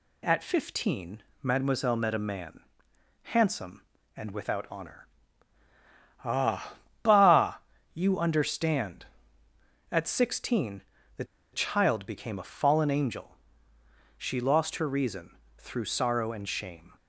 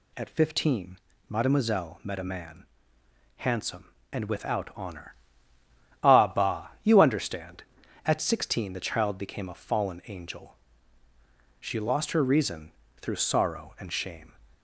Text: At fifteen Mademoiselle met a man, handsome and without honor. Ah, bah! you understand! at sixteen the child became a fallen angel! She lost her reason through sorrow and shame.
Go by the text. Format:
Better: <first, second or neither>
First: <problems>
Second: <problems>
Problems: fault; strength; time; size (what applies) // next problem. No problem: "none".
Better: second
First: pauses between "fifteen" and "Mademoiselle"; slight; at 1.2 s; 0.20 s long // pauses between "sixteen" and "the"; at 10.7 s; 0.38 s long // pauses between "the" and "child"; slight; at 11.2 s; 0.27 s long // pauses between "reason" and "through"; slight; at 15.3 s; 0.20 s long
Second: pauses between "fifteen" and "Mademoiselle"; slight; at 0.9 s; 0.28 s long // pauses between "reason" and "through"; slight; at 12.7 s; 0.28 s long